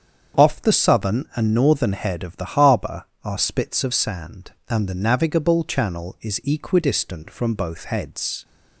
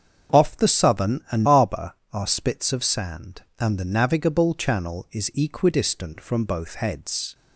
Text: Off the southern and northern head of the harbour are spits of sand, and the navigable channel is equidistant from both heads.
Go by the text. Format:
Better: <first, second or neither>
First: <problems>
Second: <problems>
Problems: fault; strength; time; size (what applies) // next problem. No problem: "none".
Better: first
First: starts louder than the rest; strong; until 1.5 s; 7.5 dB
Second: starts louder than the rest; until 1.4 s; 7 dB // skips "northern head of the"; at 1.4 s